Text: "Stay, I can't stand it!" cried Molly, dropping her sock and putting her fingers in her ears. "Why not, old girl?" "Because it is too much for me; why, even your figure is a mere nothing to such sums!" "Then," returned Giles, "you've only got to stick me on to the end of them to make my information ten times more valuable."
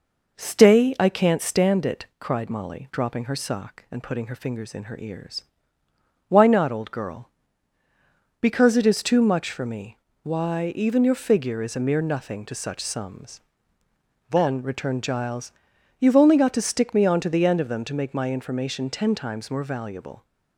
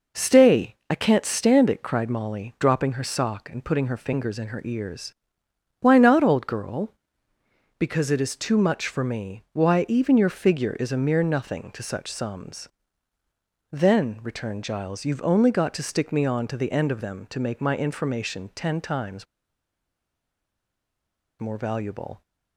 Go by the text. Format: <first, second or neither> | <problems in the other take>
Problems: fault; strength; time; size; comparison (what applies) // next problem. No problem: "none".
first | pauses between "times" and "more"; strong; at 19.2 s; 2.1 s long